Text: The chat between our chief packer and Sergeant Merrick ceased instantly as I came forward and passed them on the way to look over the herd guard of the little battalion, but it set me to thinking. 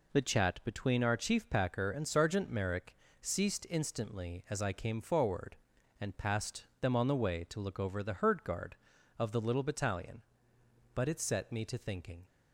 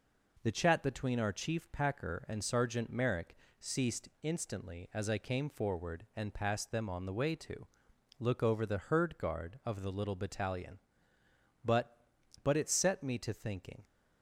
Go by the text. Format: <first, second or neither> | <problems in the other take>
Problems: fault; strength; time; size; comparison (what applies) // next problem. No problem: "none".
first | pauses between "Merrick" and "ceased"; slight; at 3.3 s; 0.24 s long; slight in the first // pauses between "to" and "look"; noticeable; at 7.6 s; 0.54 s long // says "but" twice; at 12.4 s